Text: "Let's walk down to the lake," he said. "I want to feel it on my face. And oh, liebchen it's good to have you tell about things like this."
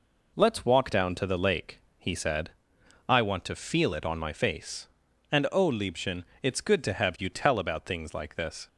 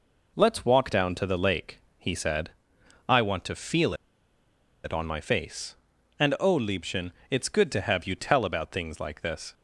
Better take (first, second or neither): first